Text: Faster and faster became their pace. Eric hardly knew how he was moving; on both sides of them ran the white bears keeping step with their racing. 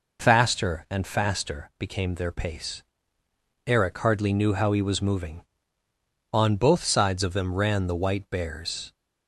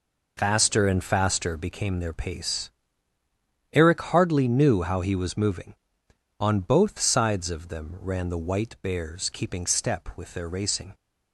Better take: second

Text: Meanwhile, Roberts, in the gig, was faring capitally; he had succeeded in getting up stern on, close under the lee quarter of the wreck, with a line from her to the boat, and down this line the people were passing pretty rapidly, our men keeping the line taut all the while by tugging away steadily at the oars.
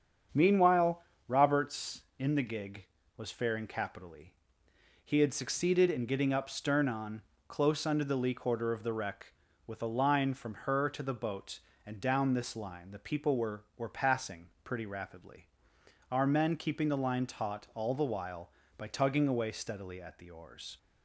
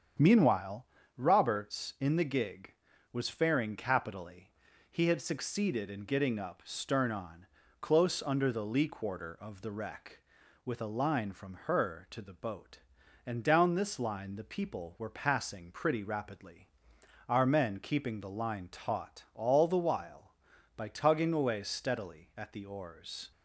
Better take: second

